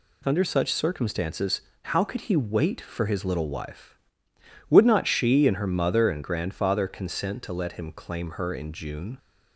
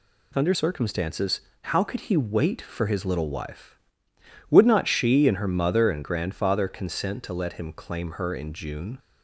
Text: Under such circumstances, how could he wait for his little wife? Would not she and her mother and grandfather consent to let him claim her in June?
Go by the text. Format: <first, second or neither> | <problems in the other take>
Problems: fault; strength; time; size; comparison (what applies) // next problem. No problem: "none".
first | skips "such"; at 0.5 s